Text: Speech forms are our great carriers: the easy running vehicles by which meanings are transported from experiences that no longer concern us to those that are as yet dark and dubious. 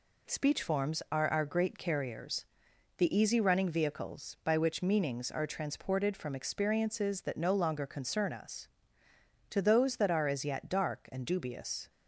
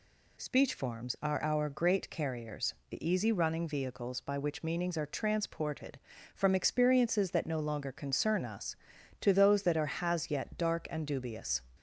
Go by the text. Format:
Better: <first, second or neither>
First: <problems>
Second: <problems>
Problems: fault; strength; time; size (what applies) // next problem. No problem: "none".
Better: first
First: none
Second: says "has" for "as"; at 9.9 s